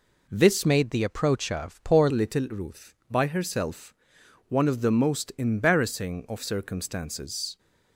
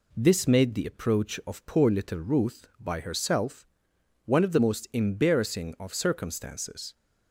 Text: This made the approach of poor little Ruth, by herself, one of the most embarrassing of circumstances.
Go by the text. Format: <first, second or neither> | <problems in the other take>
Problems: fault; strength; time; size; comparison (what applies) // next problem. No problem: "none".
second | changes voice from "made" to "poor"; from 0.6 to 2.0 s; 1.4 s long